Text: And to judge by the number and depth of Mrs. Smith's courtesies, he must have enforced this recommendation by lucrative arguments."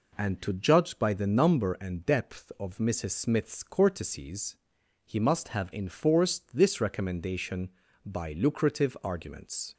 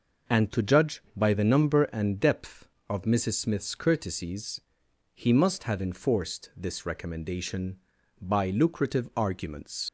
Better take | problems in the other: first | leaves "arguments" unfinished; at 9.8 s; 70 ms

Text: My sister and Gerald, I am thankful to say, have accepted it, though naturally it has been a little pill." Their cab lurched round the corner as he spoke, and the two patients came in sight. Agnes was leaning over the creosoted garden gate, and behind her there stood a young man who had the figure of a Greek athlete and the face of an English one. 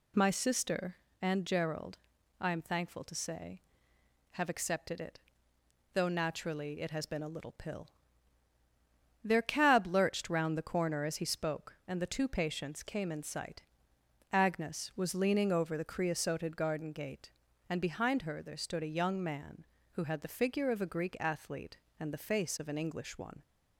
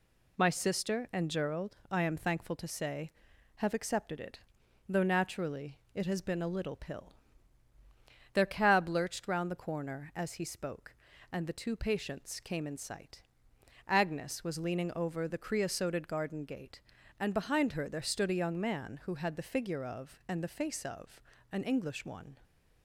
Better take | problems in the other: first | pauses between "naturally" and "it"; slight; at 5.7 s; 0.16 s long // skips "a Greek athlete"; at 20.2 s // pauses between "of" and "an"; slight; at 21.1 s; 0.32 s long

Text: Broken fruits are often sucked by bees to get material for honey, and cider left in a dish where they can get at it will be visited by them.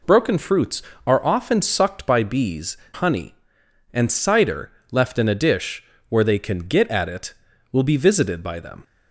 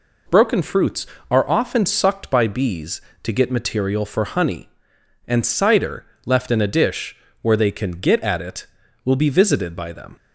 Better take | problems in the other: second | skips "to get material for"; at 2.8 s // pauses between "cider" and "left"; slight; at 4.7 s; 0.20 s long; slight in the second // pauses between "dish" and "where"; slight; at 5.8 s; 0.26 s long; slight in the second

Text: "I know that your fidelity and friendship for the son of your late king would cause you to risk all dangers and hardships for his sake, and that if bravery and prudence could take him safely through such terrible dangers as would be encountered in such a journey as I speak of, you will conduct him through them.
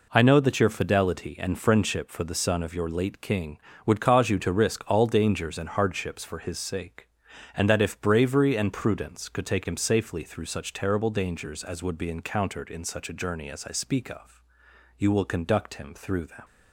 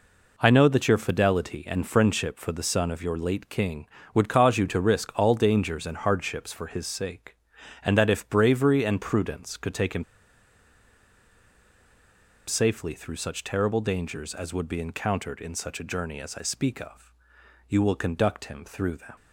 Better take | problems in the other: first | pauses between "him" and "safely"; strong; at 10.0 s; 2.4 s long

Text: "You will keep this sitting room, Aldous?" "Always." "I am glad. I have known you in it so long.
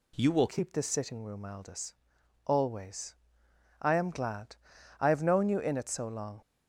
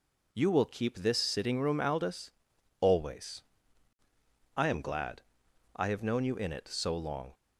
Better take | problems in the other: second | changes voice at "keep"; from 0.4 s on; 6.0 s long

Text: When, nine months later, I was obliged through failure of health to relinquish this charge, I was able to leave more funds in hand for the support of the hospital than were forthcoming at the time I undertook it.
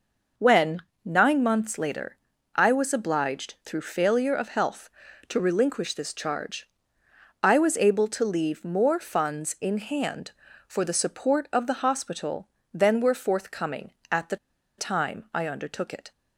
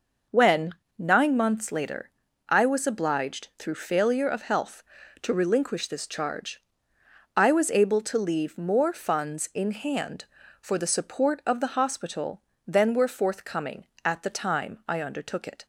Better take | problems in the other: second | pauses between "the" and "time"; at 14.3 s; 0.42 s long

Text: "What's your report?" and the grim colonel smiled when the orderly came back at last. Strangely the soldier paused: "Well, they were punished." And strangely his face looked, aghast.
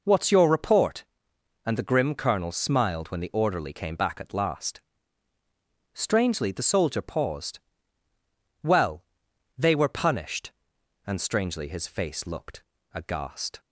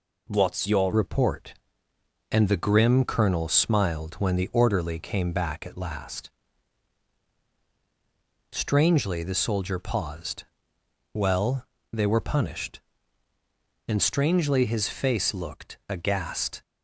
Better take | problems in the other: first | changes voice at "report"; from 0.9 s on; 15.7 s long

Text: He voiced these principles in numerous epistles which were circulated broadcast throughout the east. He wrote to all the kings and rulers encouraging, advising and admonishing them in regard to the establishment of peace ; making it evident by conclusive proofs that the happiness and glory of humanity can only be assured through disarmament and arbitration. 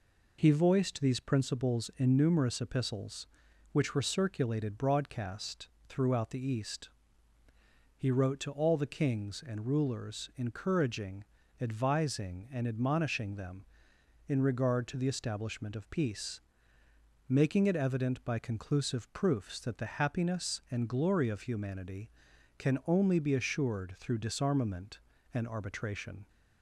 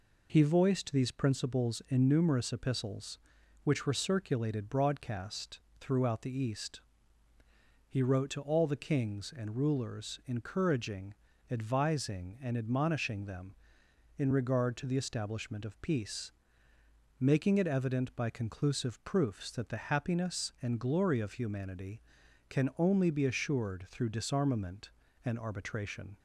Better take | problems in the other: neither | pauses between "broadcast" and "throughout"; slight; the same in both

